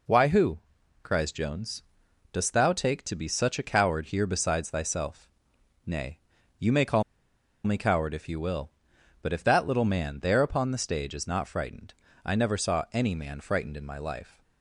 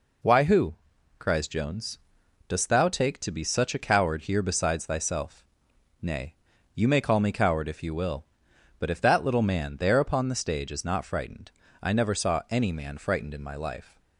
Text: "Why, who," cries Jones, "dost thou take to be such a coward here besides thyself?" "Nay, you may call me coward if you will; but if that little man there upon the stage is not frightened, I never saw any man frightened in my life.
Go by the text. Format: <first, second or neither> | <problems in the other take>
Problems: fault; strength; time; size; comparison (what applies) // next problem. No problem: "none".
second | pauses between "call" and "me"; noticeable; at 7.0 s; 0.62 s long